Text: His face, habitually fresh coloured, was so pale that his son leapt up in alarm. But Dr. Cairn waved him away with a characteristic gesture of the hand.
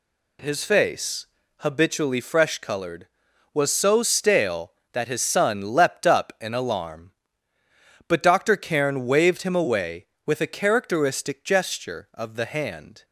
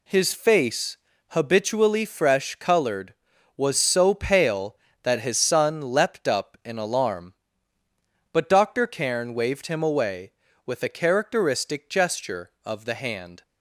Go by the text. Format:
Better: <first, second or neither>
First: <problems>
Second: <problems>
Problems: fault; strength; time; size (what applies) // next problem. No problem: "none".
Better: second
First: says "stale" for "pale"; at 4.0 s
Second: none